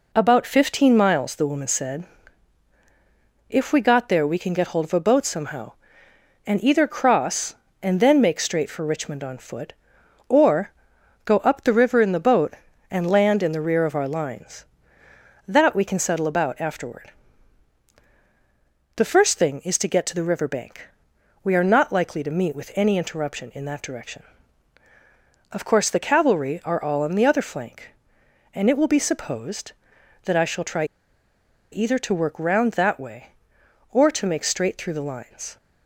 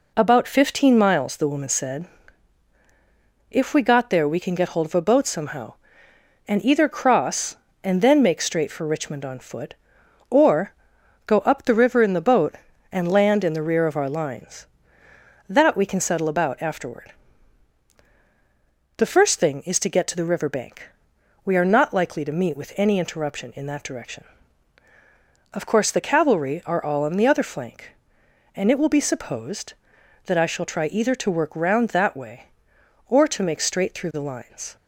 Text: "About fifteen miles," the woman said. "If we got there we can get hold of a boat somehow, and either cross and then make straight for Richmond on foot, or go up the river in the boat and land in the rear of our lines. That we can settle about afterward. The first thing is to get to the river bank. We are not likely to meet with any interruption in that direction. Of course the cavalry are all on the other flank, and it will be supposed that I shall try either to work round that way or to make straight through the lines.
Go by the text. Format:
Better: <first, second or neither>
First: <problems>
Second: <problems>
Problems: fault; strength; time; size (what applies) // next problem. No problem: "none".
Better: second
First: pauses between "or" and "go"; noticeable; at 10.6 s; 0.54 s long // pauses between "try" and "either"; noticeable; at 30.8 s; 0.87 s long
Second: pauses between "or" and "go"; noticeable; at 10.7 s; 0.54 s long